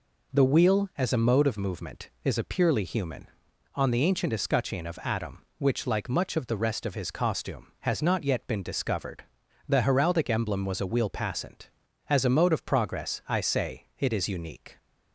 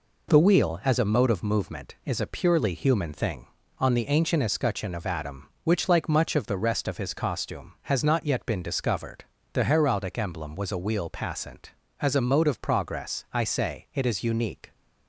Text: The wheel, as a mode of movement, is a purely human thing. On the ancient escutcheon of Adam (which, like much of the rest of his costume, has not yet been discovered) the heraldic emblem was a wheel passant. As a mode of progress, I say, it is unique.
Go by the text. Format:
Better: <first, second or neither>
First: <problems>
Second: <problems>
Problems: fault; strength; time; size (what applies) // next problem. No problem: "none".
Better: second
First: skips "thing"; at 3.4 s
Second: none